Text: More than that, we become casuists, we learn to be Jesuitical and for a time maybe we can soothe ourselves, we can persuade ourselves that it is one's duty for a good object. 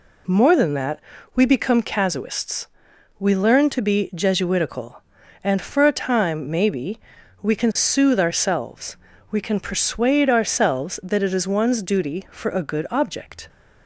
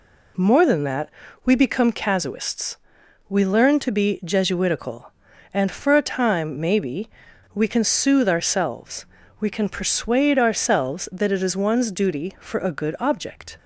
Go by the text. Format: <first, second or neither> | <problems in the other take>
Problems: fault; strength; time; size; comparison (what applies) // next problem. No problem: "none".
neither | pauses between "maybe" and "we"; the same in both